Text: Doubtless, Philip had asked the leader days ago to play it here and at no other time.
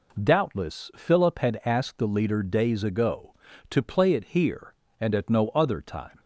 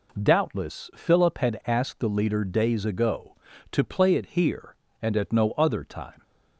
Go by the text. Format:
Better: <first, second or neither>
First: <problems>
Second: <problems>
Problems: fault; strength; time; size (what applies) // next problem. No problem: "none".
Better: neither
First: none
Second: none